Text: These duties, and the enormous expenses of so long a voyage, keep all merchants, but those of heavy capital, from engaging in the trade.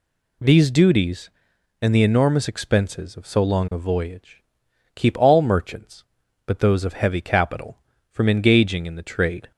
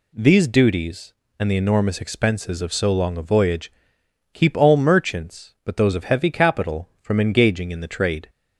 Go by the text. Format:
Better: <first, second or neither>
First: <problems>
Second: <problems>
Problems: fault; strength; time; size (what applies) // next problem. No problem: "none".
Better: neither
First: none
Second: none